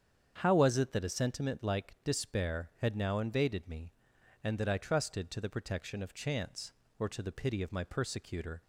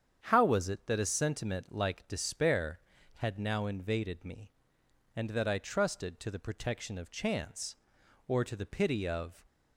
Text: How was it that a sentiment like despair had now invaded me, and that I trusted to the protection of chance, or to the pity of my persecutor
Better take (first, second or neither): first